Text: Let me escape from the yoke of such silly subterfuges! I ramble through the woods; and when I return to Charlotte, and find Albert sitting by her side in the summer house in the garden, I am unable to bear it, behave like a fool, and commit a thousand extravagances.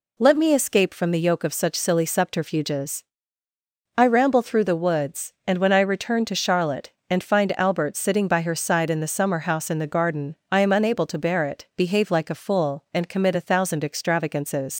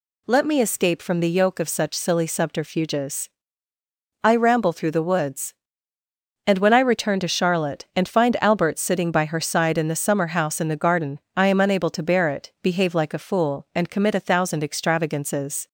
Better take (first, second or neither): second